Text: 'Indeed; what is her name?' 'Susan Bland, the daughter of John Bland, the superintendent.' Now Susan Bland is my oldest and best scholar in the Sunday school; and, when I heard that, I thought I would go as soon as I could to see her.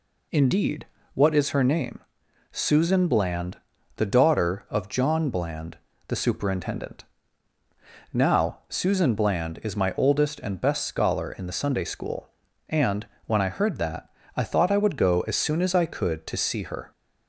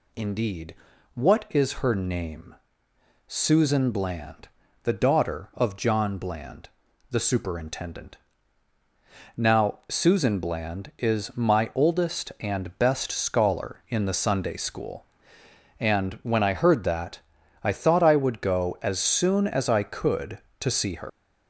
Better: first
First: none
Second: leaves "her" unfinished; at 21.0 s; 105 ms

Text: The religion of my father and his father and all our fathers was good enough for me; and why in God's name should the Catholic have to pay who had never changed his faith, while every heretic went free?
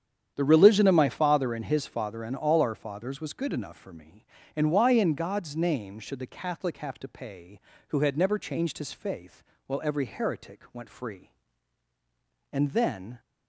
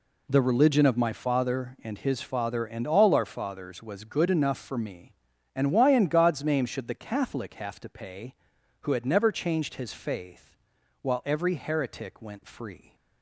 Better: second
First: starts louder than the rest; strong; until 1.3 s; 9 dB // goes on to say "And then"; noticeable; from 12.5 s on; 0.68 s long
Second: none

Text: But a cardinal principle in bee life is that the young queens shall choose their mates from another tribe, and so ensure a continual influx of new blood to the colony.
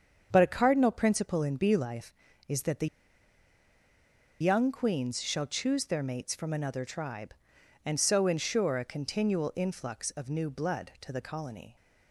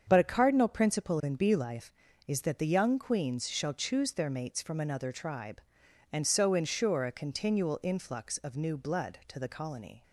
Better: second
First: starts louder than the rest; strong; until 1.3 s; 7 dB // pauses between "the" and "young"; strong; at 2.8 s; 1.5 s long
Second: starts louder than the rest; strong; until 1.0 s; 7 dB

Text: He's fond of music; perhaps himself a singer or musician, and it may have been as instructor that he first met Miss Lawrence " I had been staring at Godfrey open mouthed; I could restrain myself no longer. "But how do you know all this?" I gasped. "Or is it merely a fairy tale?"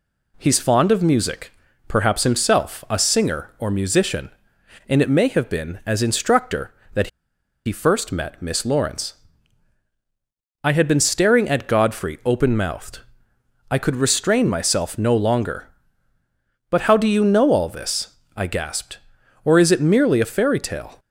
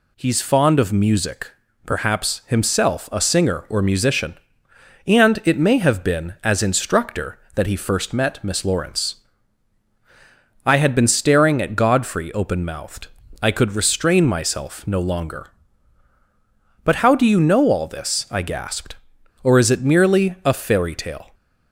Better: second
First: pauses between "that" and "he"; noticeable; at 7.0 s; 0.58 s long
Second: none

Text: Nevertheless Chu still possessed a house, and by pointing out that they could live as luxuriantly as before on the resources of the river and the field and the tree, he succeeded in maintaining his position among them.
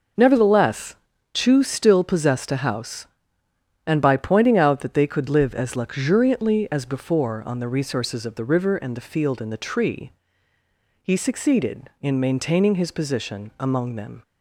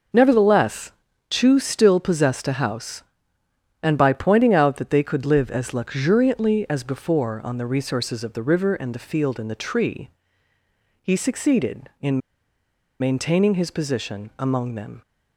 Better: first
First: pauses between "Nevertheless" and "Chu"; at 0.9 s; 0.38 s long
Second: pauses between "Nevertheless" and "Chu"; at 0.9 s; 0.38 s long // pauses between "in" and "maintaining"; noticeable; at 12.1 s; 0.80 s long

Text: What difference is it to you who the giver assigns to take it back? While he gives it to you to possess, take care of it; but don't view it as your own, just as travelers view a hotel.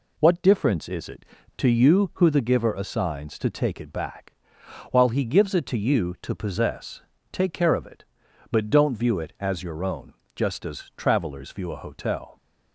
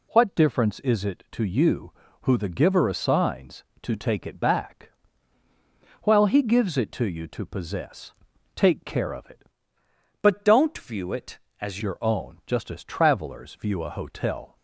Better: first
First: none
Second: changes voice from "but" to "as"; from 10.2 to 11.7 s; 1.5 s long

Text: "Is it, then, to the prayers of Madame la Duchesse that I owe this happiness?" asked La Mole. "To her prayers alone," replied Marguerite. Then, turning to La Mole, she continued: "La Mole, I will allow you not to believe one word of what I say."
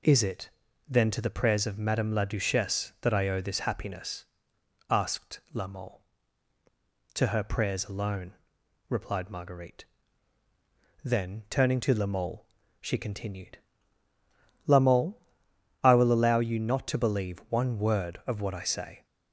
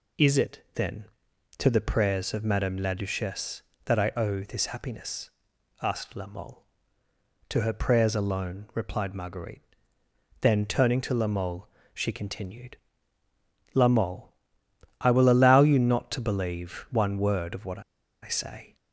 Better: first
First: none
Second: pauses between "what" and "I"; at 17.7 s; 0.42 s long

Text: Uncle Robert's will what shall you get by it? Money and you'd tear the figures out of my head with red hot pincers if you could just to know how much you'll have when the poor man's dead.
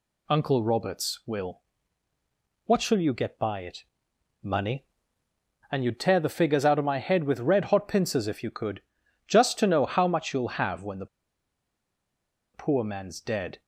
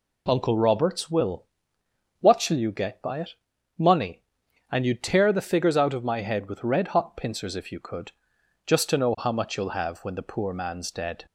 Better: second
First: pauses between "will" and "what"; at 1.6 s; 1.0 s long // pauses between "could" and "just"; noticeable; at 8.8 s; 0.46 s long // pauses between "the" and "poor"; strong; at 11.0 s; 1.4 s long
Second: pauses between "will" and "what"; noticeable; at 1.4 s; 0.74 s long // pauses between "could" and "just"; noticeable; at 8.1 s; 0.54 s long

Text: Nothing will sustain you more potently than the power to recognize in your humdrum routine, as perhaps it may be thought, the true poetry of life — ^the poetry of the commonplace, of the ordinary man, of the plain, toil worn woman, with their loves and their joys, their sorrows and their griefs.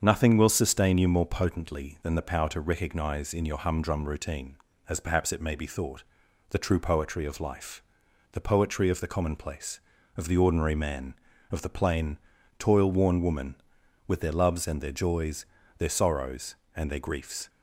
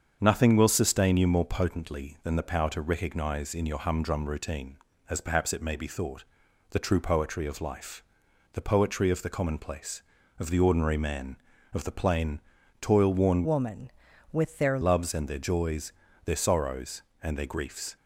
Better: first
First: starts louder than the rest; strong; until 1.0 s; 7.5 dB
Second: starts louder than the rest; strong; until 1.2 s; 7.5 dB // changes voice from "woman" to "their"; from 13.4 to 14.7 s; 1.3 s long

